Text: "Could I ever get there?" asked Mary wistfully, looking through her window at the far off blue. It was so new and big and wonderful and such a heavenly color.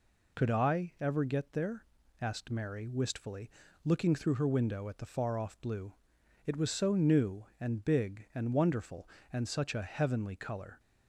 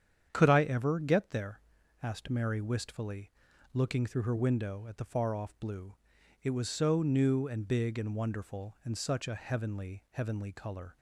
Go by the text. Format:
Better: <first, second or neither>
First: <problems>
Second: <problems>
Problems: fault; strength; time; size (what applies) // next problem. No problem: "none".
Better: first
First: none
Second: starts louder than the rest; strong; until 1.3 s; 8.5 dB // says "heavenly" twice; at 10.1 s